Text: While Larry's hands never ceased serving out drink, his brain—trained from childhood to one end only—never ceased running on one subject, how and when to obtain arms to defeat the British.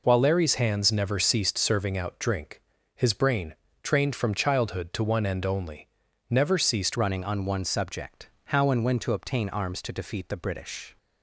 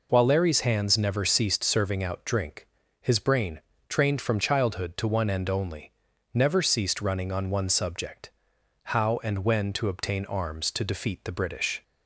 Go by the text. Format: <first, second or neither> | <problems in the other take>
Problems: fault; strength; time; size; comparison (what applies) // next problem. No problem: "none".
second | changes voice at "running"; from 6.9 s on; 4.0 s long